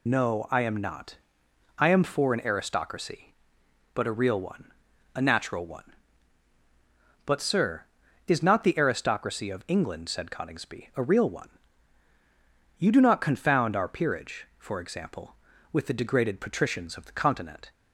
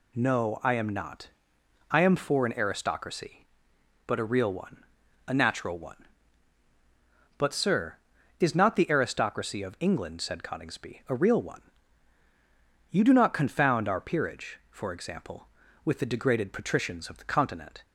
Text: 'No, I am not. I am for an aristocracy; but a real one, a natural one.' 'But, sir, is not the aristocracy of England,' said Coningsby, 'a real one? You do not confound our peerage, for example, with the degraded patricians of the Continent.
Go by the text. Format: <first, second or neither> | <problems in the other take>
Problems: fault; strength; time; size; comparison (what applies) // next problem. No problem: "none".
second | loses the start of "No"; at 0.0 s; 30 ms